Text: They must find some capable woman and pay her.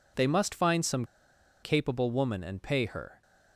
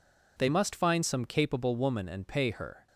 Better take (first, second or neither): second